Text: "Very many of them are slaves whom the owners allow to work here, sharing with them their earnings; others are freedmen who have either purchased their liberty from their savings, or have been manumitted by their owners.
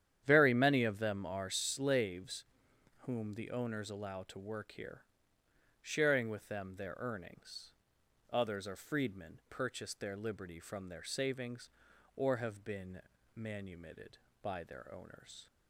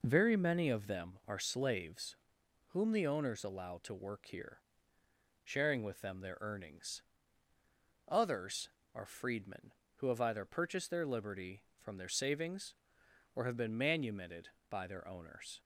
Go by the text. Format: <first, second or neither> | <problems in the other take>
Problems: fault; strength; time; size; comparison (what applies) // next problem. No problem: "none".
second | starts louder than the rest; strong; until 1.2 s; 10 dB // pauses between "slaves" and "whom"; noticeable; at 2.4 s; 0.54 s long; noticeable in the second // skips "who have either"; at 9.4 s // pauses between "been" and "manumitted"; slight; at 13.0 s; 0.36 s long